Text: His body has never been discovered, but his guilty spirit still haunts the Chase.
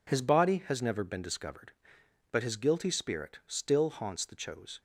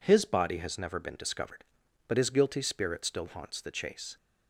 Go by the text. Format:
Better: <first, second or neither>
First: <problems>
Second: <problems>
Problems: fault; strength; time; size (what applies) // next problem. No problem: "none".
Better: second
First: says "Chose" for "Chase"; at 4.3 s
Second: none